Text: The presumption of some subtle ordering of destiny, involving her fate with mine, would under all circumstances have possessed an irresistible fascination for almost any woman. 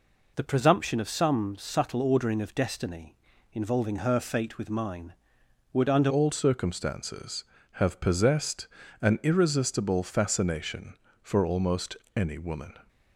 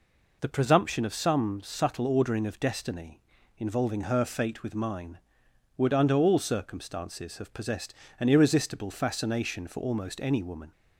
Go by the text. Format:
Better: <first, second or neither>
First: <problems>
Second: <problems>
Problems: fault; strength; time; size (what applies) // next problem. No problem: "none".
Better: second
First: changes voice at "all"; from 6.0 s on; 6.7 s long // pauses between "possessed" and "an"; slight; at 8.6 s; 0.34 s long // pauses between "almost" and "any"; slight; at 11.9 s; 0.22 s long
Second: pauses between "possessed" and "an"; slight; at 7.9 s; 0.28 s long